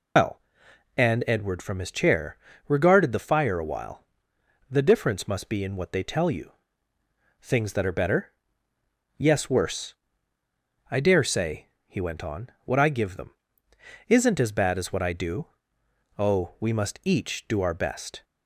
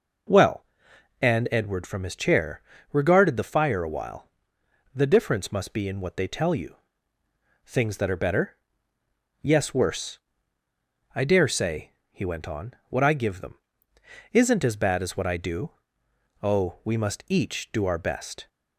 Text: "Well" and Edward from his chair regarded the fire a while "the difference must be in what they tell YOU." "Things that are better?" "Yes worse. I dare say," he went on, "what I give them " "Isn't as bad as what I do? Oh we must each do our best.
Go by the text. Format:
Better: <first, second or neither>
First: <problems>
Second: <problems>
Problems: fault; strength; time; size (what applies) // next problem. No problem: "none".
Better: second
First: loses the start of "Well"; at 0.1 s; 120 ms // pauses between "chair" and "regarded"; slight; at 2.3 s; 0.32 s long // pauses between "while" and "the"; noticeable; at 4.0 s; 0.66 s long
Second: pauses between "chair" and "regarded"; slight; at 2.5 s; 0.32 s long // pauses between "while" and "the"; noticeable; at 4.2 s; 0.66 s long